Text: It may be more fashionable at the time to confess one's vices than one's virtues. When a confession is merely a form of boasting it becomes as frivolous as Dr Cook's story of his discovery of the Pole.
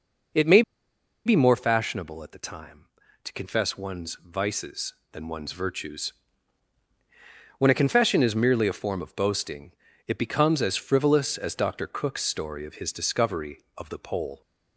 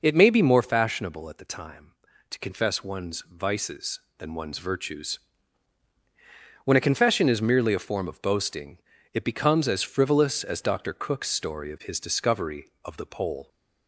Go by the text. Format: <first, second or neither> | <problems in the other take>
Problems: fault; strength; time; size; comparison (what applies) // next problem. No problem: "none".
second | pauses between "may" and "be"; noticeable; at 0.6 s; 0.64 s long // pauses between "boasting" and "it"; slight; at 9.7 s; 0.34 s long; slight in the second